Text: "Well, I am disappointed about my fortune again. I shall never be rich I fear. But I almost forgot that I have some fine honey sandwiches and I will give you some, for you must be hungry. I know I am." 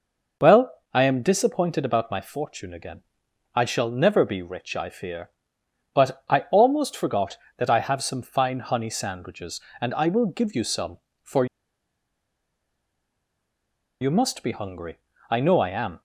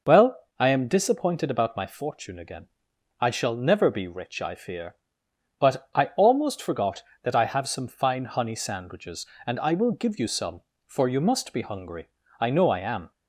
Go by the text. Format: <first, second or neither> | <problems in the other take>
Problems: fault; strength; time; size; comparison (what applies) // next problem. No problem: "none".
second | pauses between "for" and "you"; strong; at 11.4 s; 2.5 s long